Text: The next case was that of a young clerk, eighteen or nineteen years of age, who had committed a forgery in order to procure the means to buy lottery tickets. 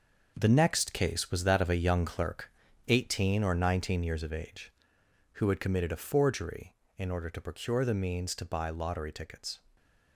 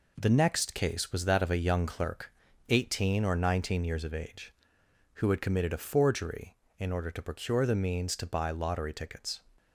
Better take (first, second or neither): second